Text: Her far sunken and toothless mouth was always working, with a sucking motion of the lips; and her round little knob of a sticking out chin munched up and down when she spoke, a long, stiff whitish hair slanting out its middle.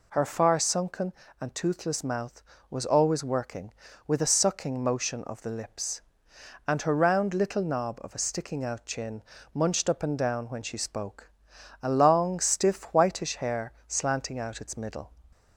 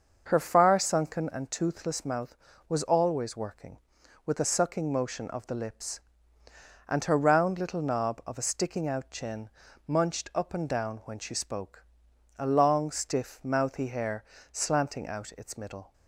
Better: first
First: pauses between "chin" and "munched"; slight; at 9.2 s; 0.32 s long // pauses between "hair" and "slanting"; slight; at 13.7 s; 0.16 s long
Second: starts louder than the rest; until 1.2 s; 6.5 dB // pauses between "chin" and "munched"; at 9.4 s; 0.38 s long // says "mouthy" for "whitish"; at 13.4 s // pauses between "hair" and "slanting"; slight; at 14.2 s; 0.26 s long

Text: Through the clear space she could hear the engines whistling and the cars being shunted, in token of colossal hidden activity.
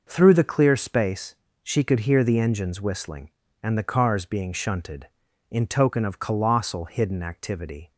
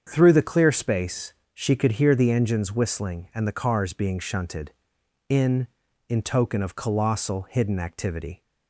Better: first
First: pauses between "space" and "she"; slight; at 1.3 s; 0.26 s long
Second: starts louder than the rest; strong; until 1.0 s; 7.5 dB // pauses between "space" and "she"; slight; at 1.3 s; 0.18 s long // says "in" twice; at 6.0 s

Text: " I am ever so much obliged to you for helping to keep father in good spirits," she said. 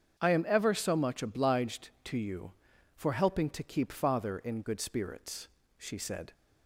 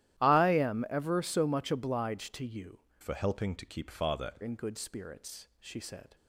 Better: first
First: starts louder than the rest; strong; until 1.2 s; 7.5 dB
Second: starts louder than the rest; strong; until 1.2 s; 13.5 dB // changes voice from "for" to "father"; from 3.0 to 4.3 s; 1.3 s long

